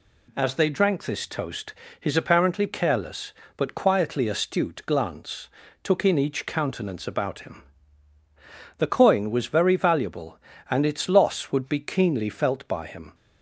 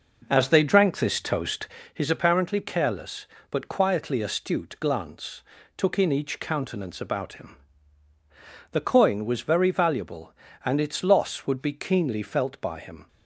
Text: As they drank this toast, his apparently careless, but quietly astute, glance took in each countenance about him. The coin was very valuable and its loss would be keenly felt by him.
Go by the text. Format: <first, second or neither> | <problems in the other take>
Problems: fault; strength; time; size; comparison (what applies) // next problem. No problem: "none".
first | starts louder than the rest; noticeable; until 1.8 s; 5.5 dB // pauses between "glance" and "took"; slight; at 5.4 s; 0.36 s long; slight in the first